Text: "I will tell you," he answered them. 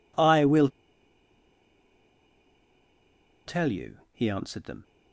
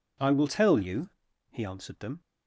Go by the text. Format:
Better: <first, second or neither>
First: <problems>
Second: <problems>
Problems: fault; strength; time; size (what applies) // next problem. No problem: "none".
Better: second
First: pauses between "will" and "tell"; strong; at 0.6 s; 2.7 s long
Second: none